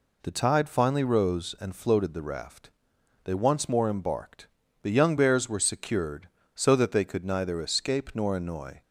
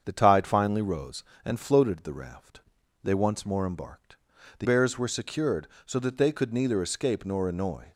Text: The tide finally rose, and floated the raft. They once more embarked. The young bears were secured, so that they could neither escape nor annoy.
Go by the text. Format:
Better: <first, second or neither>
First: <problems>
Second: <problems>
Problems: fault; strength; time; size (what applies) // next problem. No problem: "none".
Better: first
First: none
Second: starts louder than the rest; strong; until 1.0 s; 7.5 dB // skips "young"; at 4.6 s